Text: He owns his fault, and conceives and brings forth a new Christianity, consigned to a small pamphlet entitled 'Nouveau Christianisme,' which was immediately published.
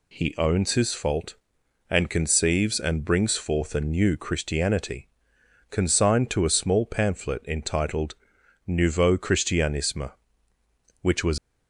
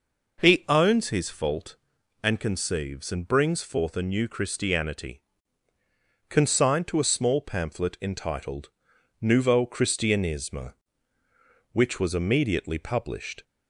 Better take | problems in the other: second | pauses between "entitled" and "Nouveau"; noticeable; at 8.1 s; 0.52 s long; noticeable in the second // stops before "immediately published"; at 11.3 s

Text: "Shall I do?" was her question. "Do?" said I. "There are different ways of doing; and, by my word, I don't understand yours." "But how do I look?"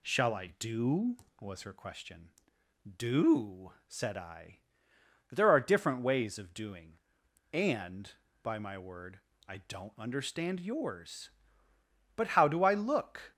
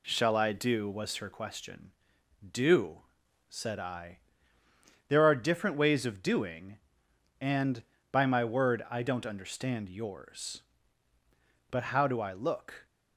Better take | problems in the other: neither | none

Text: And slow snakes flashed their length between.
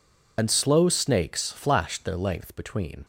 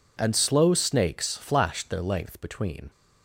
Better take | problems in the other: second | loses the start of "And"; at 0.3 s; 65 ms

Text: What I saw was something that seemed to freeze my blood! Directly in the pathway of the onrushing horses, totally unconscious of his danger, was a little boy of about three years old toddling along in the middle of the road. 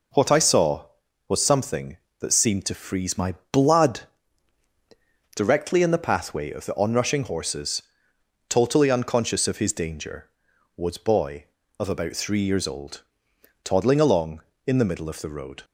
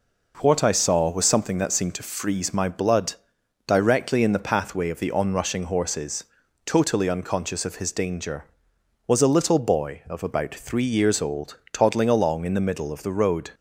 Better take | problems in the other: second | pauses between "my" and "blood"; slight; at 3.3 s; 0.20 s long // skips "a little"; at 10.9 s // pauses between "old" and "toddling"; noticeable; at 13.0 s; 0.60 s long; slight in the second

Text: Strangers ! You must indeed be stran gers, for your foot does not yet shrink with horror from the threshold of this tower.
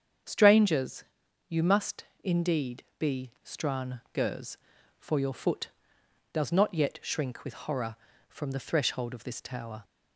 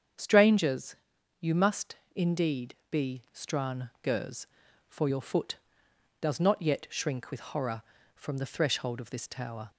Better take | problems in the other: neither | starts louder than the rest; strong; the same in both // pauses between "must" and "indeed"; slight; the same in both

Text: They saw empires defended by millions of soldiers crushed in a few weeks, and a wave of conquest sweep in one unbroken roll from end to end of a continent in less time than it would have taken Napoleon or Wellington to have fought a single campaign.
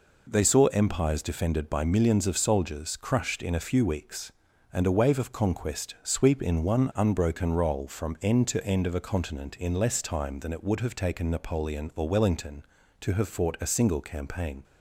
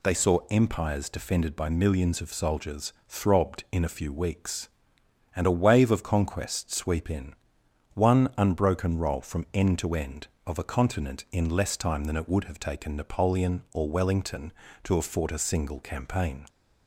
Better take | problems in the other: first | says "throbbed" for "crushed"; at 3.0 s // pauses between "in" and "one"; noticeable; at 7.3 s; 0.58 s long

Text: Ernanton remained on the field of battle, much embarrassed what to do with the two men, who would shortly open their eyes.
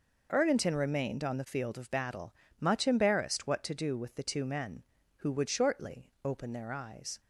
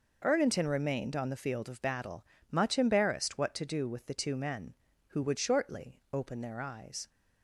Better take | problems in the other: neither | none

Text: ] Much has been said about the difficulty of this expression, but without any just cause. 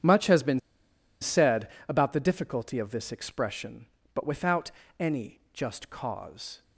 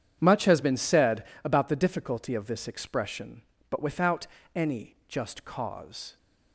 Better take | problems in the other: second | starts louder than the rest; strong; until 1.6 s; 9 dB; strong in the second // pauses between "been" and "said"; noticeable; at 0.5 s; 0.62 s long // pauses between "said" and "about"; slight; at 1.6 s; 0.22 s long; slight in the second // pauses between "without" and "any"; slight; at 4.7 s; 0.28 s long; slight in the second

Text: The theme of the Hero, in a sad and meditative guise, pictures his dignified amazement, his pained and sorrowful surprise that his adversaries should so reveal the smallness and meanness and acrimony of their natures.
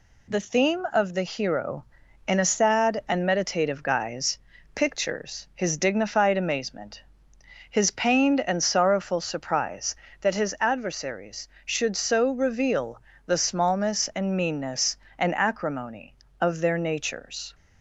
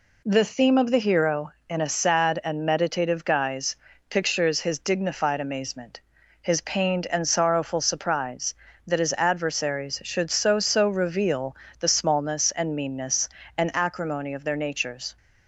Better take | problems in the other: first | says "so" twice; at 10.6 s // pauses between "reveal" and "the"; slight; at 11.5 s; 0.24 s long; slight in the first

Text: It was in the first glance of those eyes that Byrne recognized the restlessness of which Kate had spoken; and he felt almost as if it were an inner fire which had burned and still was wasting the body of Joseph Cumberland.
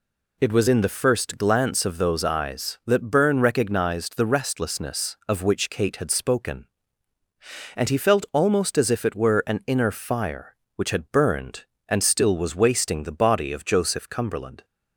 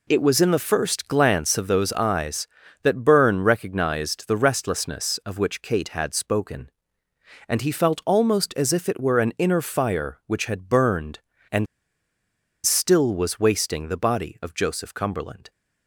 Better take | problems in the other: first | pauses between "and" and "still"; at 11.6 s; 1.0 s long

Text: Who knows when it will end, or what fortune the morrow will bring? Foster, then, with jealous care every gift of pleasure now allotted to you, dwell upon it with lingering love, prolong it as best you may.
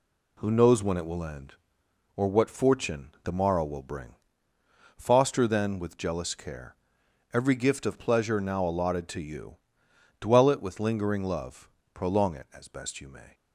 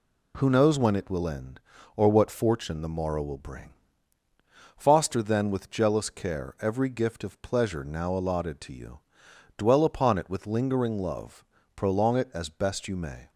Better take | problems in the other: second | pauses between "care" and "every"; noticeable; at 6.7 s; 0.60 s long // skips "upon"; at 10.4 s

